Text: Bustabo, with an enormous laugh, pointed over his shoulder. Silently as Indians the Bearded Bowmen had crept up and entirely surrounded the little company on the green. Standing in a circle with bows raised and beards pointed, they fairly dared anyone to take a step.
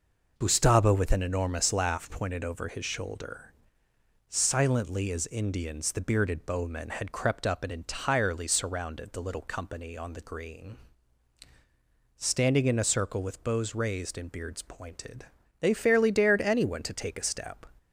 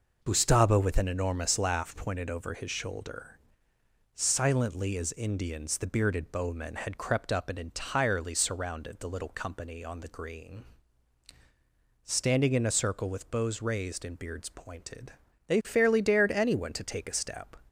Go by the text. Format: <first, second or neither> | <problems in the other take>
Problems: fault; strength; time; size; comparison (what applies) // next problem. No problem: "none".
neither | none